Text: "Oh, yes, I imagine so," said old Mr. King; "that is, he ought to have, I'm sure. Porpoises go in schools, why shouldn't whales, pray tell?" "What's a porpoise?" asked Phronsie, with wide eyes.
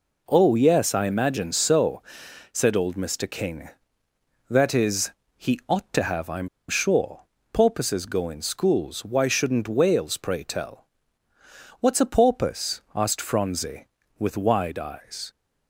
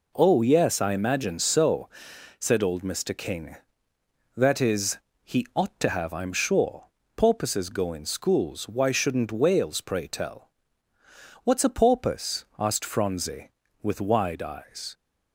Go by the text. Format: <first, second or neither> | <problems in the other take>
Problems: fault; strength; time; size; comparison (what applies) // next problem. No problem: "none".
second | pauses between "I'm" and "sure"; slight; at 6.4 s; 0.20 s long